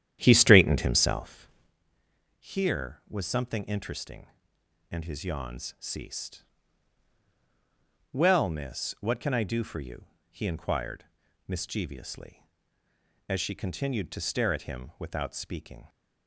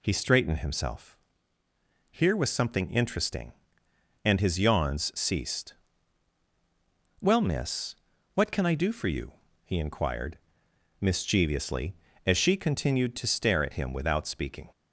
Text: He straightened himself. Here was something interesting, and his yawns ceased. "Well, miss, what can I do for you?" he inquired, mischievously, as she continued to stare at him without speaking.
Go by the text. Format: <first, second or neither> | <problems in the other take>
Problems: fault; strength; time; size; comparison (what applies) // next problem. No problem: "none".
second | starts louder than the rest; strong; until 1.7 s; 10.5 dB